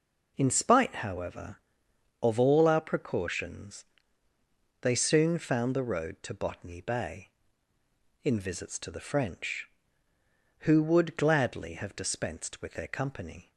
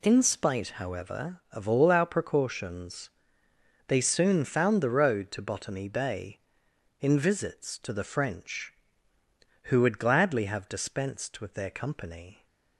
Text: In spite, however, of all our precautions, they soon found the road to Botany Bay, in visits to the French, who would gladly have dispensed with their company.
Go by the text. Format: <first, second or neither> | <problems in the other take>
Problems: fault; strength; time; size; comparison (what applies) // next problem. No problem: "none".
neither | none